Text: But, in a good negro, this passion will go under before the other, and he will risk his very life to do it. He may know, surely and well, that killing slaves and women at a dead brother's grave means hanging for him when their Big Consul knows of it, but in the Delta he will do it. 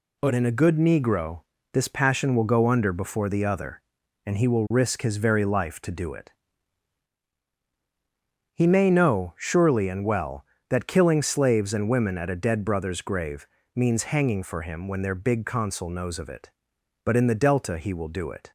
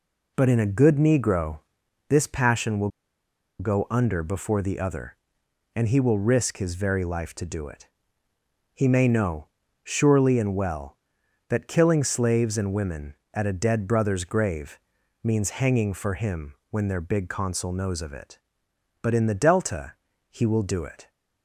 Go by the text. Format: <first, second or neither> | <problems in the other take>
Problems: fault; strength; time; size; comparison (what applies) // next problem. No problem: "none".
first | pauses between "will" and "go"; noticeable; at 2.8 s; 0.69 s long // pauses between "grave" and "means"; at 14.7 s; 0.44 s long; slight in the first // pauses between "Delta" and "he"; slight; at 19.9 s; 0.36 s long